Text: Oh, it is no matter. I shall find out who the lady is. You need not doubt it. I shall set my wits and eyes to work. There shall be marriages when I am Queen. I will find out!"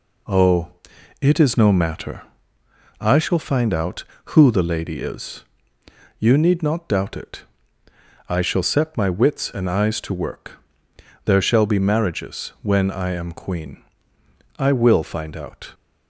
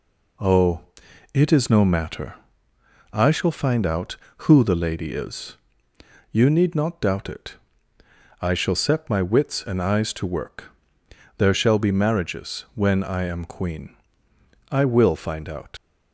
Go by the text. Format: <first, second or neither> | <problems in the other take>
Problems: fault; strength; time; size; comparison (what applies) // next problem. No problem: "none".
first | leaves "out" unfinished; at 15.7 s; 90 ms